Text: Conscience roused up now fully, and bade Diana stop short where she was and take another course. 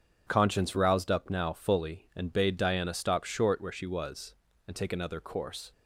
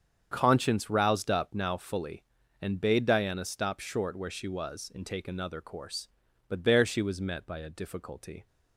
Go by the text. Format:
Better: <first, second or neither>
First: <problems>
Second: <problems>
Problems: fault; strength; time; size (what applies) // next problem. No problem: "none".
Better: first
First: starts louder than the rest; strong; until 1.2 s; 8 dB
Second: starts louder than the rest; strong; until 1.3 s; 7.5 dB // goes on to say "But there she was met by a difficulty"; strong; from 6.4 s on; 1.9 s long